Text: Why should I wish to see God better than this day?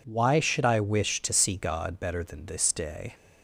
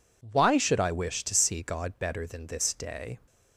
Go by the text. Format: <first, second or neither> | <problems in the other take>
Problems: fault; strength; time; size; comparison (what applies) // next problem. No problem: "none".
neither | none